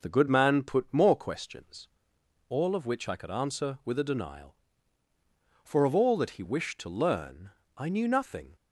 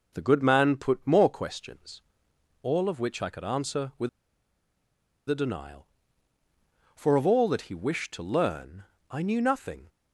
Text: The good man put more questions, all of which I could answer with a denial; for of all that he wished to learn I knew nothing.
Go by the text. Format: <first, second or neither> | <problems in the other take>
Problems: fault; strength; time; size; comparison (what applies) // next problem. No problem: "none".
first | pauses between "with" and "a"; at 4.0 s; 1.1 s long // pauses between "learn" and "I"; slight; at 8.8 s; 0.26 s long; slight in the first